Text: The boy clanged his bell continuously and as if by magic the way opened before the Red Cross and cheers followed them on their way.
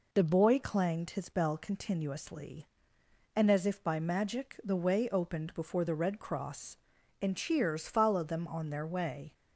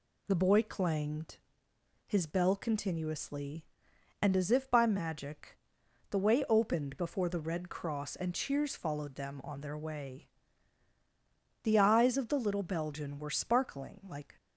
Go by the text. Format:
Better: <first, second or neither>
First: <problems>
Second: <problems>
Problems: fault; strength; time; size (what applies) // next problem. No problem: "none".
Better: first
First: none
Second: pauses between "clanged" and "his"; noticeable; at 1.3 s; 0.70 s long // pauses between "magic" and "the"; noticeable; at 5.5 s; 0.53 s long // goes on to say "The eyes of the little Belgian were sparkling like"; strong; from 11.6 s on; 2.7 s long